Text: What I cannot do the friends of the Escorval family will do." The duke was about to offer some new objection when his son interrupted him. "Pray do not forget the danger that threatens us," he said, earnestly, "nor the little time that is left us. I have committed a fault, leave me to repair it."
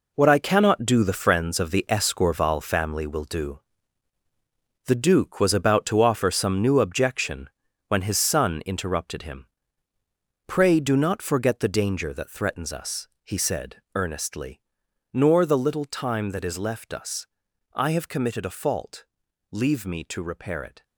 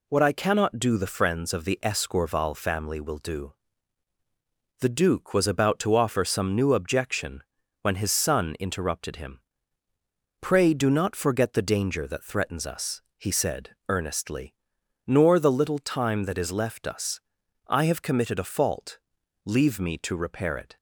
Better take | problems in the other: second | gets quieter; strong; throughout; 9.5 dB // pauses between "objection" and "when"; at 7.4 s; 0.38 s long; also in the second

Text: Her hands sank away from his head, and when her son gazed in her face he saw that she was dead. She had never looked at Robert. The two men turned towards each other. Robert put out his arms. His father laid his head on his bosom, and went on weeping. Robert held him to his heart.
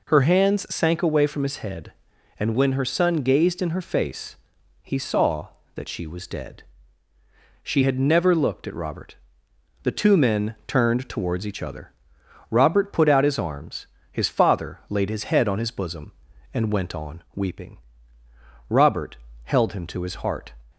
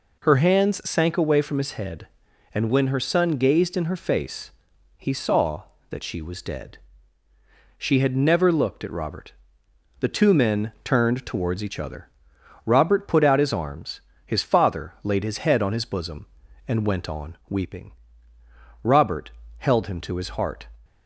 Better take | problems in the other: neither | pauses between "face" and "he"; noticeable; the same in both // pauses between "Robert" and "held"; slight; the same in both

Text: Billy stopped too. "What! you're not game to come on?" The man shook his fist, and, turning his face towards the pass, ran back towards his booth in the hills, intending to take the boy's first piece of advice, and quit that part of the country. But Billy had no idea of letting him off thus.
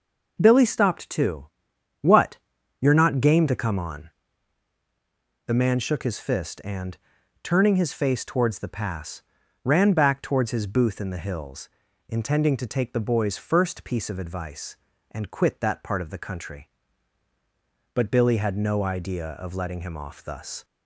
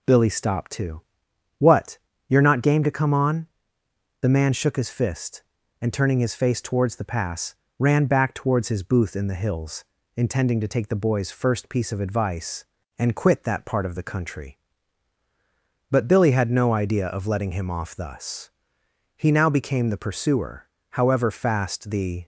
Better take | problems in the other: first | goes on to say "He now became the pursuer However fast the"; strong; from 19.1 s on; 3.1 s long

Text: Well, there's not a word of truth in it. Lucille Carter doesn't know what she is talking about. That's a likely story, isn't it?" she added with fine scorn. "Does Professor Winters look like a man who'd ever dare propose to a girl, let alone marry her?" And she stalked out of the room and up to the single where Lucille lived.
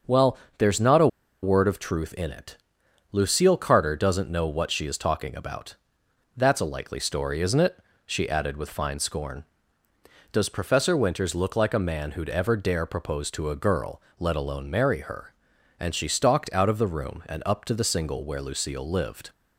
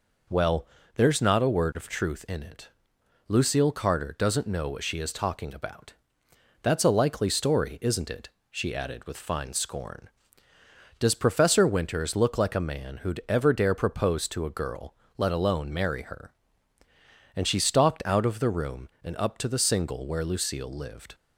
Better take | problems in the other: second | starts louder than the rest; until 1.6 s; 6.5 dB // pauses between "a" and "word"; slight; at 1.0 s; 0.35 s long

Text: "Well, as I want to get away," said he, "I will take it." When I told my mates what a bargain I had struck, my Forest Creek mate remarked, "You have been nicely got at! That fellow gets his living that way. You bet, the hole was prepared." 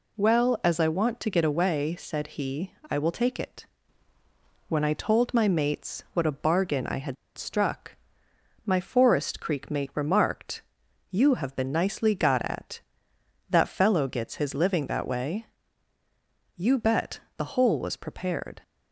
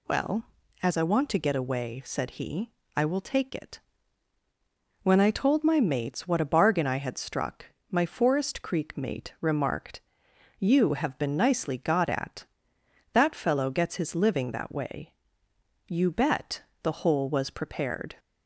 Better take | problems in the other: second | pauses between "had" and "struck"; slight; at 7.1 s; 0.21 s long

